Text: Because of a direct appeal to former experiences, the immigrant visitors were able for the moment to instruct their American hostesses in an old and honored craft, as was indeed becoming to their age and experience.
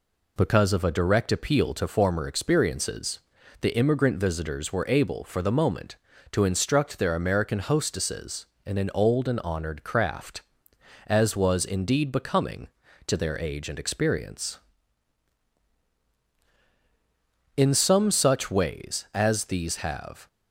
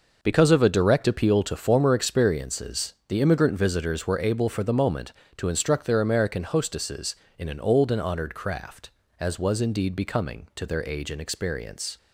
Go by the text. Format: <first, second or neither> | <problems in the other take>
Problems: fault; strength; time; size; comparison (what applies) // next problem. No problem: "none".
second | goes on to say "In some such ways as these have"; strong; from 17.5 s on; 2.7 s long